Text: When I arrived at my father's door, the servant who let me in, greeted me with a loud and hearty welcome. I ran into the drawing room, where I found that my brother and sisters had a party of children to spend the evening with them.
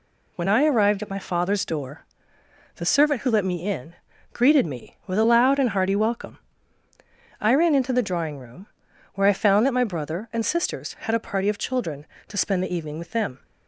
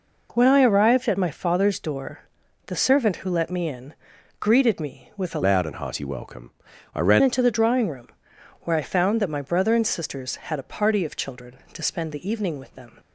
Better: first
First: none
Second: changes voice from "loud" to "ran"; from 5.4 to 7.2 s; 1.8 s long

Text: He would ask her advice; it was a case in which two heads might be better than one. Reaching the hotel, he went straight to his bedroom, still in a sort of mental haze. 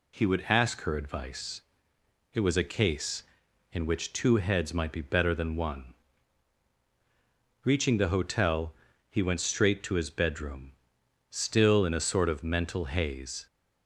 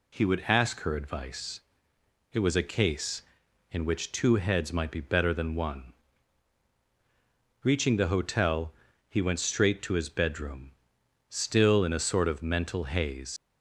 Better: first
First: none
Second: leaves "haze" unfinished; at 13.3 s; 90 ms

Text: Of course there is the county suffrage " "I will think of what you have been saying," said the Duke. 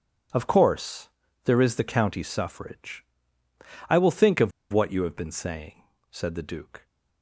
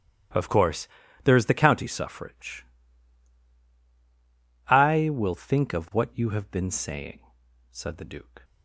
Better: second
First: pauses between "course" and "there"; slight; at 1.0 s; 0.34 s long // pauses between "of" and "what"; slight; at 4.5 s; 0.20 s long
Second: pauses between "course" and "there"; slight; at 0.8 s; 0.36 s long

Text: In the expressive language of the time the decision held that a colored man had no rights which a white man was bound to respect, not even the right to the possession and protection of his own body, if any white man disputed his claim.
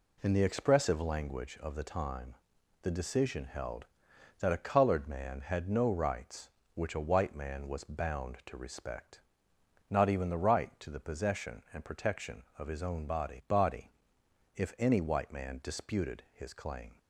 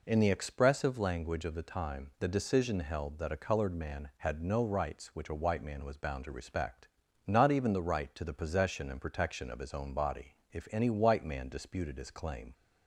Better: second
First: pauses between "time" and "the"; noticeable; at 2.3 s; 0.48 s long // says "body" twice; at 13.4 s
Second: none

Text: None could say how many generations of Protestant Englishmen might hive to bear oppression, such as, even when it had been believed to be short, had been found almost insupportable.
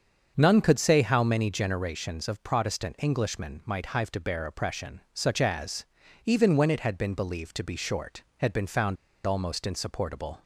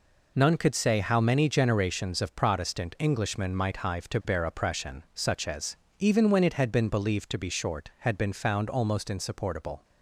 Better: second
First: starts louder than the rest; until 1.3 s; 7 dB // pauses between "found" and "almost"; slight; at 8.9 s; 0.30 s long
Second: none

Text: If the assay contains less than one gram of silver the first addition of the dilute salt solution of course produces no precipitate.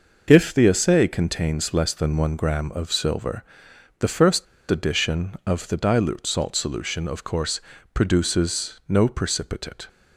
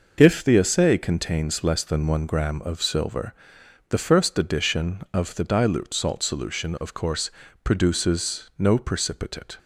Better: second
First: pauses between "silver" and "the"; noticeable; at 3.4 s; 0.54 s long // pauses between "first" and "addition"; slight; at 4.4 s; 0.24 s long // pauses between "course" and "produces"; slight; at 7.6 s; 0.32 s long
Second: pauses between "silver" and "the"; noticeable; at 3.3 s; 0.54 s long // pauses between "course" and "produces"; slight; at 7.3 s; 0.32 s long

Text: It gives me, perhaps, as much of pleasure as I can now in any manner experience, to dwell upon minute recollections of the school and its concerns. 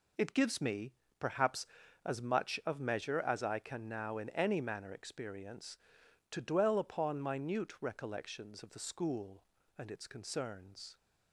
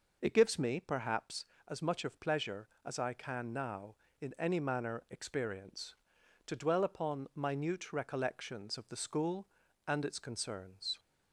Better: second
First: says "measure" for "pleasure"; at 2.7 s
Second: none

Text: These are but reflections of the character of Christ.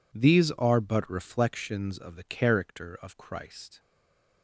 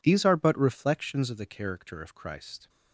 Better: second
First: stays silent after the last word; slight; from 3.7 s on; 0.7 s long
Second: none

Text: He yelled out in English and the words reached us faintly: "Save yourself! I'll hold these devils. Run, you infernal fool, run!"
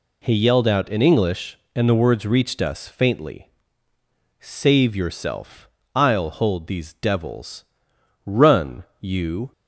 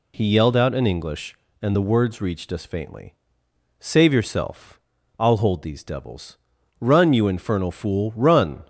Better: second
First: stops before "infernal fool run"; at 9.5 s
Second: none

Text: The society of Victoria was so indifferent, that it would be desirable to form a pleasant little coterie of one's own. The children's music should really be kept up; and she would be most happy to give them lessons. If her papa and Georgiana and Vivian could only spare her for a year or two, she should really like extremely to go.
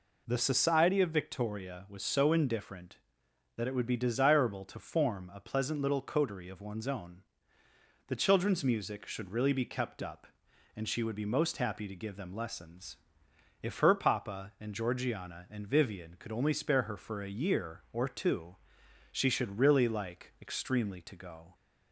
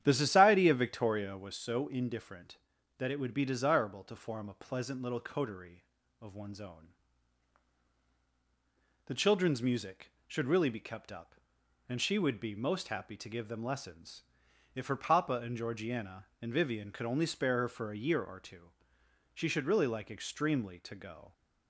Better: first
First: none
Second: starts louder than the rest; strong; until 1.6 s; 10 dB

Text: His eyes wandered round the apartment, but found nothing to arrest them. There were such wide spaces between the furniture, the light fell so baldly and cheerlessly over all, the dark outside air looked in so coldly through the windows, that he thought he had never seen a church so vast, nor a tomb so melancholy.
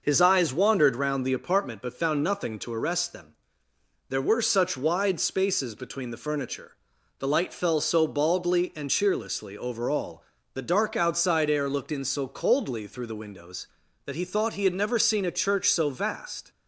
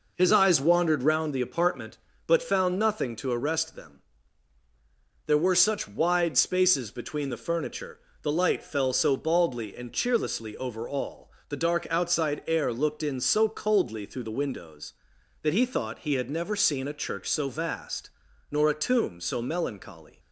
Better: second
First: stops before "nor a tomb so melancholy"; at 16.5 s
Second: none

